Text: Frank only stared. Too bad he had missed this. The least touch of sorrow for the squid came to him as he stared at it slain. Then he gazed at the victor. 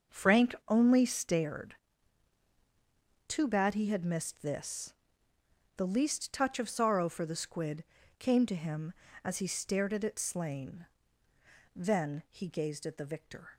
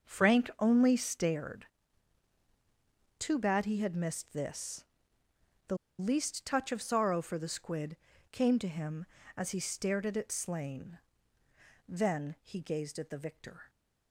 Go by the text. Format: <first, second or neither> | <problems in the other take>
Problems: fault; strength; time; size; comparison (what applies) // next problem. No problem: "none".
first | starts louder than the rest; until 1.1 s; 6 dB; also in the first // pauses between "The" and "least"; slight; at 5.7 s; 0.23 s long // pauses between "squid" and "came"; slight; at 7.9 s; 0.36 s long; slight in the first